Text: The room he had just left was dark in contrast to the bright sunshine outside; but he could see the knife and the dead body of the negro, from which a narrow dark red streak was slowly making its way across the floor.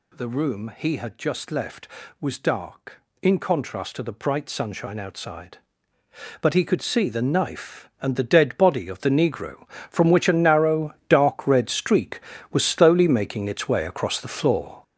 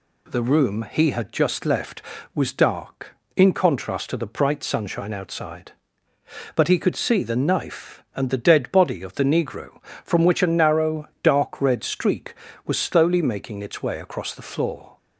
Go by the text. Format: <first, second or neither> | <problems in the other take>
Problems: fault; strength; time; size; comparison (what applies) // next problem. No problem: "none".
second | gets louder; strong; throughout; 8.5 dB // pauses between "narrow" and "dark"; slight; at 10.9 s; 0.16 s long; slight in the second